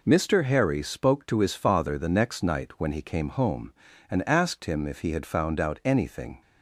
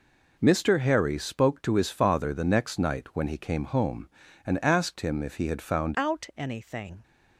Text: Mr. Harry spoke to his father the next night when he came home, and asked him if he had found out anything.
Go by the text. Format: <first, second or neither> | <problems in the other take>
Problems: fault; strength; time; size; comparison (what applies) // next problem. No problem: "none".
first | changes voice at "out"; from 5.9 s on; 1.1 s long